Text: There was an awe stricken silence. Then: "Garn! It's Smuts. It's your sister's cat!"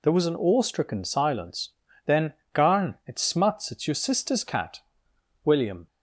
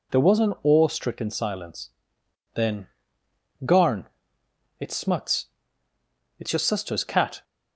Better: second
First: goes on to say "William"; slight; from 5.4 s on; 0.44 s long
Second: none

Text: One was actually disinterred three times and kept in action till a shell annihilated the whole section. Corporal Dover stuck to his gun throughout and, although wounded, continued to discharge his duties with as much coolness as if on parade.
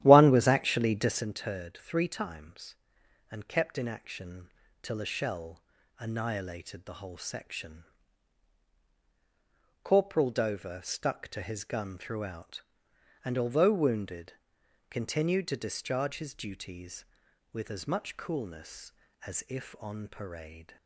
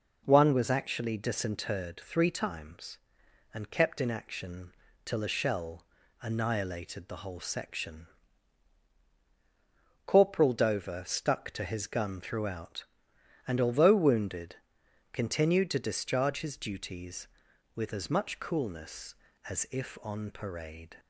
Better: second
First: starts louder than the rest; strong; until 1.2 s; 12.5 dB // pauses between "action" and "till"; slight; at 4.4 s; 0.32 s long // pauses between "shell" and "annihilated"; slight; at 5.6 s; 0.36 s long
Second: pauses between "action" and "till"; slight; at 4.7 s; 0.32 s long // pauses between "shell" and "annihilated"; slight; at 5.8 s; 0.36 s long

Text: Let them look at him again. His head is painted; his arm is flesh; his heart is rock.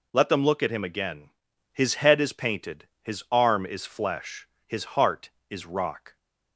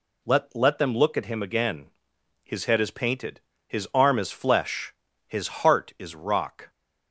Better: first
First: none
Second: says "Let" twice; at 0.5 s

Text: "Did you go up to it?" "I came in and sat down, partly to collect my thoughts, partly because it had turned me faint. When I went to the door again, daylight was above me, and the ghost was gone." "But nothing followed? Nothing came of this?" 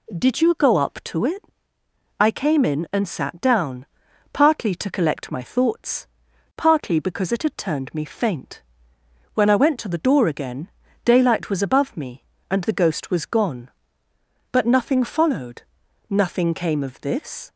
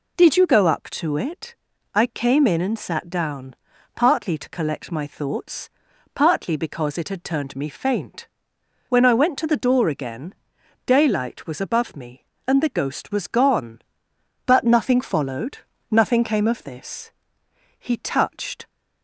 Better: first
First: none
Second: goes on to say "He touched"; noticeable; from 17.7 s on; 0.88 s long

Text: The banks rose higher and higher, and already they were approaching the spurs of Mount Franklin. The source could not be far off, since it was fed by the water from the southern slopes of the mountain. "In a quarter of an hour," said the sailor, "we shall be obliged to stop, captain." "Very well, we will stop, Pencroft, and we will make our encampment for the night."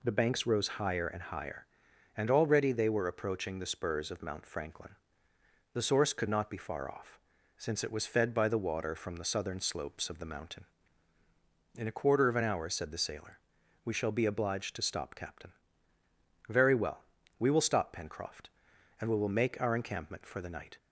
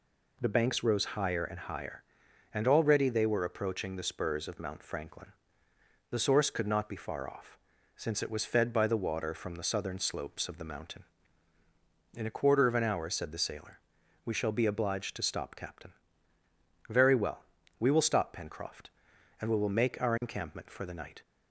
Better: neither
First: none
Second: none

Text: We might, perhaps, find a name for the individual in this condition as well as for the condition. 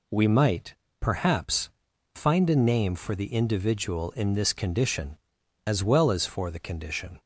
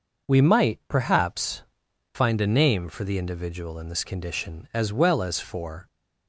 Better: first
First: none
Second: stops before "the condition"; at 5.8 s

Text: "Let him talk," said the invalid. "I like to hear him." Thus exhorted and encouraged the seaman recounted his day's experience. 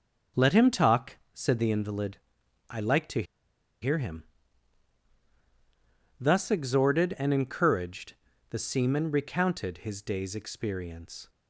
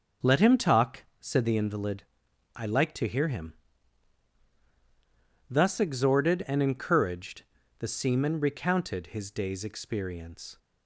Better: second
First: starts louder than the rest; until 1.5 s; 6 dB // pauses between "to" and "hear"; noticeable; at 3.2 s; 0.58 s long // pauses between "encouraged" and "the"; slight; at 8.1 s; 0.34 s long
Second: starts louder than the rest; until 1.4 s; 6 dB // pauses between "encouraged" and "the"; slight; at 7.4 s; 0.34 s long

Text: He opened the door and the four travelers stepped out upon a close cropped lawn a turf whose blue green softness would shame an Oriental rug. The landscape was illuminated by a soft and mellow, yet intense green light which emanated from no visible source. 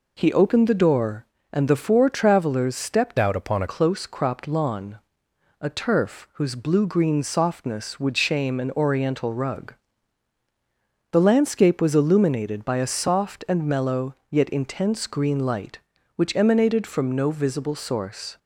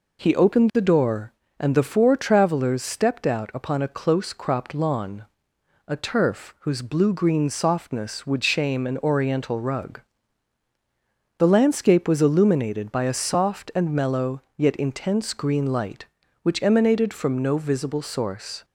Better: second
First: changes voice from "out" to "a"; from 3.1 to 3.6 s; 0.5 s long // pauses between "lawn" and "a"; noticeable; at 4.9 s; 0.60 s long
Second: pauses between "lawn" and "a"; noticeable; at 5.2 s; 0.60 s long

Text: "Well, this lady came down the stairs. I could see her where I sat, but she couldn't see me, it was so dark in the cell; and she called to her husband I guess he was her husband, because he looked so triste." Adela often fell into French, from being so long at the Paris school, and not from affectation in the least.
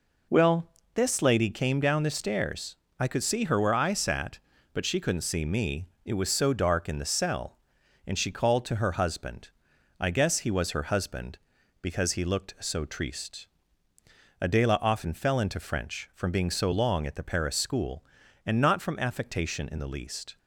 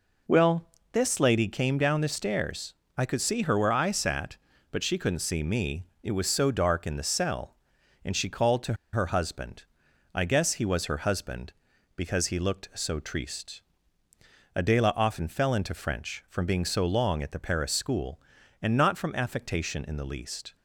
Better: first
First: pauses between "husband" and "I"; noticeable; at 9.4 s; 0.50 s long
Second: pauses between "to" and "her"; slight; at 8.7 s; 0.18 s long // pauses between "husband" and "I"; noticeable; at 9.6 s; 0.50 s long

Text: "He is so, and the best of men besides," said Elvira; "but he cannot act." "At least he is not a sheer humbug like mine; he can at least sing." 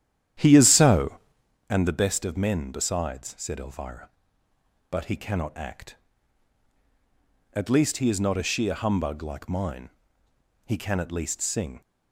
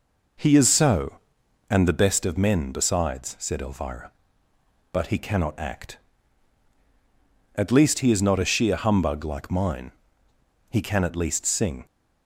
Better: second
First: starts louder than the rest; strong; until 1.5 s; 10.5 dB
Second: none

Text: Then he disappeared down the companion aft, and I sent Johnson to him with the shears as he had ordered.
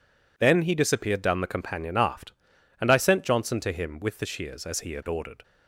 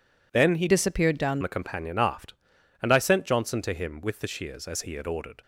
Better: first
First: none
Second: changes voice from "disappeared" to "down"; from 0.6 to 1.4 s; 0.8 s long

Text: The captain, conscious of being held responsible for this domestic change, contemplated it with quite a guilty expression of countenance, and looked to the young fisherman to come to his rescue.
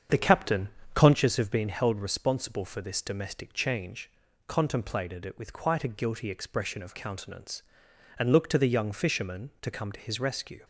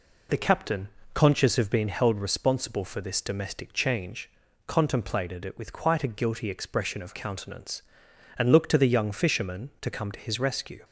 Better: second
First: starts louder than the rest; strong; until 1.2 s; 7.5 dB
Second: none

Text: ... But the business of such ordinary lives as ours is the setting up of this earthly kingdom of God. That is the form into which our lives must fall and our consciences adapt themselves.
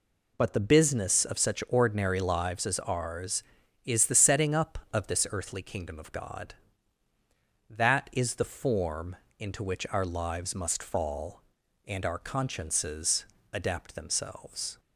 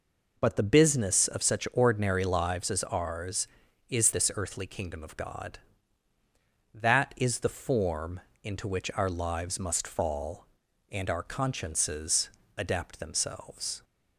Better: first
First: pauses between "form" and "into"; slight; at 9.1 s; 0.22 s long // pauses between "consciences" and "adapt"; slight; at 13.2 s; 0.26 s long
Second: skips "the setting up of"; at 4.1 s // pauses between "form" and "into"; slight; at 8.1 s; 0.22 s long // pauses between "consciences" and "adapt"; slight; at 12.2 s; 0.26 s long

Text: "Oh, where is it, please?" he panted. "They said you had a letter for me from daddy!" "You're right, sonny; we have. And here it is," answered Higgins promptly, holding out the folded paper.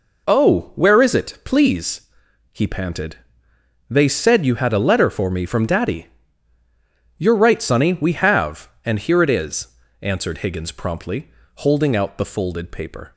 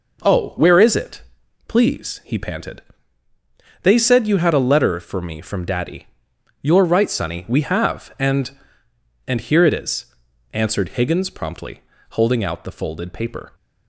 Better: first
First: none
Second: says "And" twice; at 9.2 s

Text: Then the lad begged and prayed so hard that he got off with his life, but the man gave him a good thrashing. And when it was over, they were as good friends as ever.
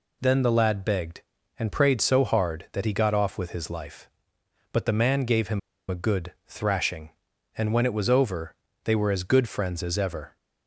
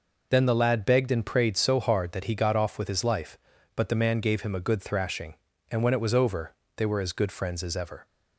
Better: second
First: pauses between "him" and "a"; slight; at 5.5 s; 0.31 s long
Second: none

